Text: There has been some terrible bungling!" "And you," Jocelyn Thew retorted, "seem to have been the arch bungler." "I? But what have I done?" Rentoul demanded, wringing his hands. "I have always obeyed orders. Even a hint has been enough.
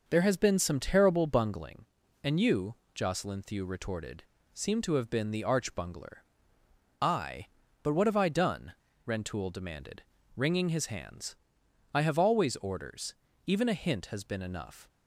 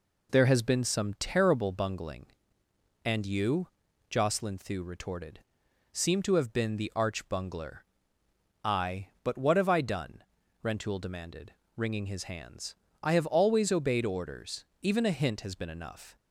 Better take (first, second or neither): second